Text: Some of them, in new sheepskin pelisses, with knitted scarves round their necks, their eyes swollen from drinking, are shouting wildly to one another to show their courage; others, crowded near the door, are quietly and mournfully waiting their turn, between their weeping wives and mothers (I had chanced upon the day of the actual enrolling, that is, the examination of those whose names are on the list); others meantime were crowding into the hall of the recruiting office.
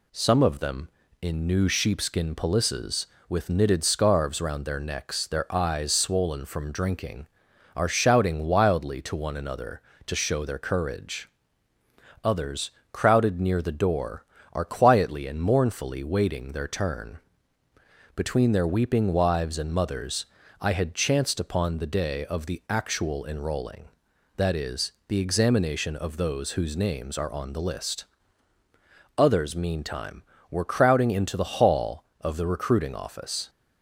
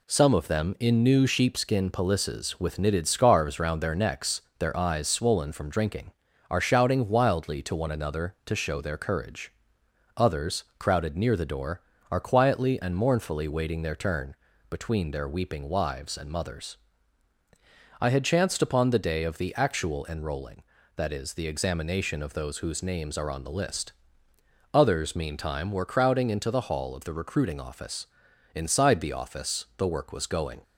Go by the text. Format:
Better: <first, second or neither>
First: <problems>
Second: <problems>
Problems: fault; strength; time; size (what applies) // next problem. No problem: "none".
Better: first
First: none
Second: goes on to say "Inside the office the work was going"; strong; from 28.5 s on; 2.0 s long